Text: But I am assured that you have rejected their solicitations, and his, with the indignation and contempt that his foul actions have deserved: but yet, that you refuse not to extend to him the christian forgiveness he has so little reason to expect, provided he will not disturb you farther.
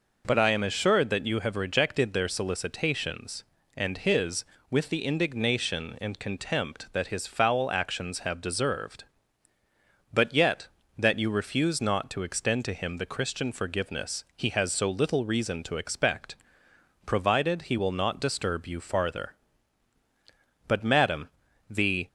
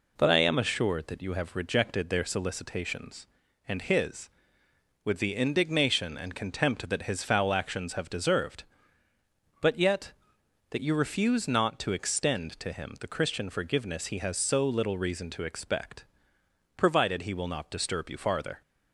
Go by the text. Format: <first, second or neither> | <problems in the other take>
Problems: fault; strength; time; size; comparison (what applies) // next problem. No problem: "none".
second | goes on to say "But Madam the"; from 20.6 s on; 1.3 s long